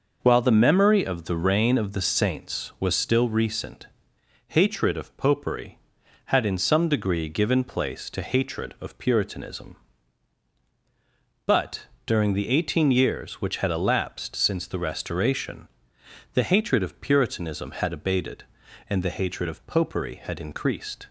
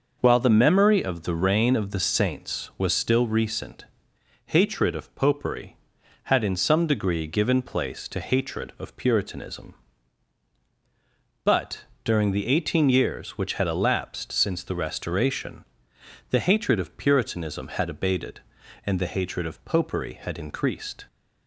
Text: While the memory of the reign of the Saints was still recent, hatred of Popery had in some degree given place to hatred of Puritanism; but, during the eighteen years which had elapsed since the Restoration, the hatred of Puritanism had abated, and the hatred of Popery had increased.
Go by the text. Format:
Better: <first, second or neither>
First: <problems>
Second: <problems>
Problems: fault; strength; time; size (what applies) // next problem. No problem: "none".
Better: neither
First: none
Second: none